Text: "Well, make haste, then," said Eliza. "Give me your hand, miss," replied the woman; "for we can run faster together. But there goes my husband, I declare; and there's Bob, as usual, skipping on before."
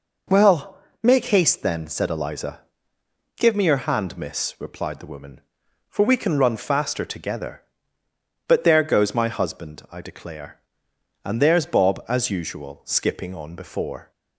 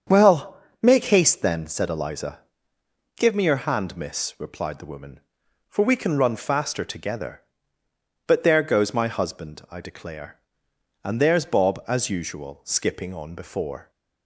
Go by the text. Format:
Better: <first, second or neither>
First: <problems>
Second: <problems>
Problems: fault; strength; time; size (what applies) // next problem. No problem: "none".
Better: first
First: none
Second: starts louder than the rest; strong; until 1.7 s; 7.5 dB